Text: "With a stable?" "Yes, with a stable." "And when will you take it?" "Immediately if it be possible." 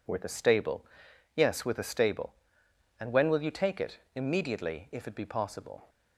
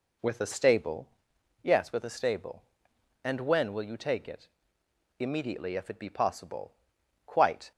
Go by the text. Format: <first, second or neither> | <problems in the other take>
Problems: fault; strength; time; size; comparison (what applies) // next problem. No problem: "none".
first | goes on to say "Quite"; slight; from 7.2 s on; 0.46 s long